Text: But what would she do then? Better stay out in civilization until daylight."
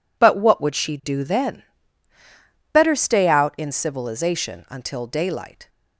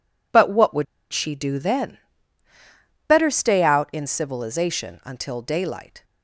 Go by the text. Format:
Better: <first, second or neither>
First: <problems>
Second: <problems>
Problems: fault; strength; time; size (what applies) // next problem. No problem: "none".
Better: first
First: none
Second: pauses between "would" and "she"; slight; at 0.8 s; 0.28 s long